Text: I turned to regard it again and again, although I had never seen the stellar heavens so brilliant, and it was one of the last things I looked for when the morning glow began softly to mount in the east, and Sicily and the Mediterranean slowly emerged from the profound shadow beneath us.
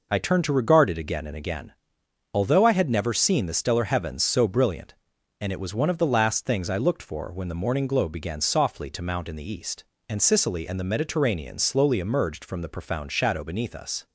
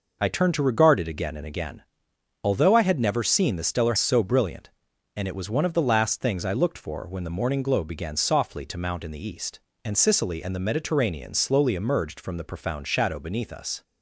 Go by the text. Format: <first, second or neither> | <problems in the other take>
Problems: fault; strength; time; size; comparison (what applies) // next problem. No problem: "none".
first | skips "heavens"; at 3.9 s